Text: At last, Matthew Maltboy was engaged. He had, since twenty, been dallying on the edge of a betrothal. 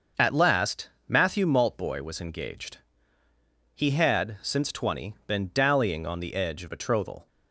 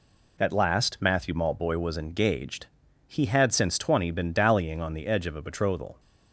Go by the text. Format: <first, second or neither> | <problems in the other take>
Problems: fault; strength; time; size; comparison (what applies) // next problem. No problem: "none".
second | starts louder than the rest; until 1.3 s; 6.5 dB // skips "a"; at 6.6 s